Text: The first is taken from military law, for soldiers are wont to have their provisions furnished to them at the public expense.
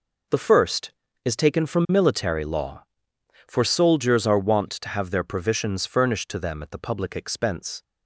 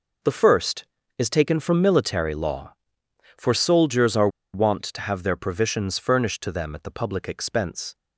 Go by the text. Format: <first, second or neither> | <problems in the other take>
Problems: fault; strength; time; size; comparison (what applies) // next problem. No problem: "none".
first | pauses between "are" and "wont"; slight; at 4.2 s; 0.25 s long